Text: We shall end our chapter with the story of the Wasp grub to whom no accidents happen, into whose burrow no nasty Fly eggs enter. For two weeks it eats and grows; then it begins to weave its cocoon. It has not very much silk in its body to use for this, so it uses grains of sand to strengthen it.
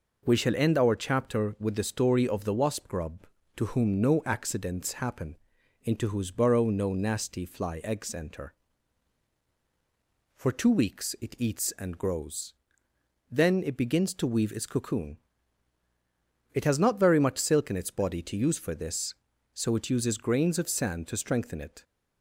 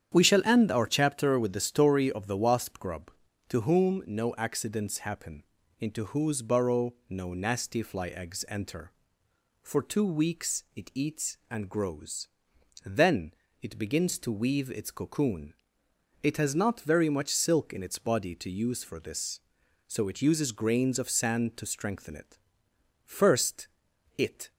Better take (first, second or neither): first